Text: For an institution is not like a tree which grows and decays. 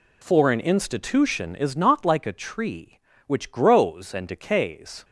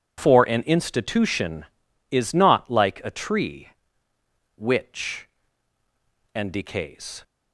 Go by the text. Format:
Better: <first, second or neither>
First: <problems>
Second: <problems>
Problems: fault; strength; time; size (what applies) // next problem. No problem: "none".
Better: first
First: none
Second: skips "grows"; at 5.8 s